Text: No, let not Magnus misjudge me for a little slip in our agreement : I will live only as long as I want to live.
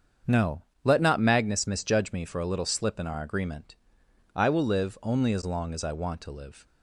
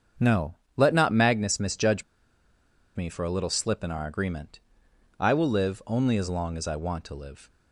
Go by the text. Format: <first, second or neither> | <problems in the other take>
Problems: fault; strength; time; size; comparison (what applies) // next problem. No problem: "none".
first | starts louder than the rest; strong; until 1.4 s; 7 dB; strong in the first // pauses between "misjudge" and "me"; noticeable; at 2.0 s; 0.92 s long